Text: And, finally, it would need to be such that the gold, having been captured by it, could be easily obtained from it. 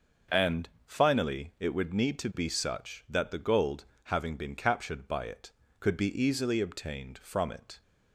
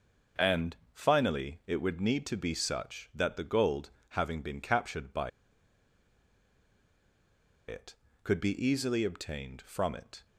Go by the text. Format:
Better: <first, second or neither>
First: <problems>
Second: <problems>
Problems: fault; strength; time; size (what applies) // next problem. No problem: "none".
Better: first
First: starts louder than the rest; until 1.4 s; 6.5 dB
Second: starts louder than the rest; until 1.5 s; 6 dB // pauses between "by" and "it"; strong; at 5.2 s; 2.3 s long